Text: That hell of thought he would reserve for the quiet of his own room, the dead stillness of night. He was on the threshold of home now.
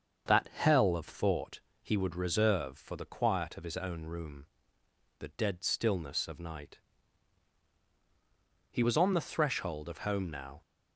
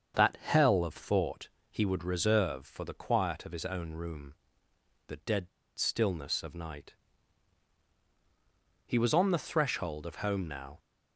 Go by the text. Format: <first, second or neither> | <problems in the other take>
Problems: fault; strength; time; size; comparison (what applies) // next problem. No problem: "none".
first | starts louder than the rest; until 1.2 s; 7 dB; also in the first // pauses between "thought" and "he"; slight; at 1.4 s; 0.20 s long; slight in the first // pauses between "dead" and "stillness"; slight; at 5.4 s; 0.28 s long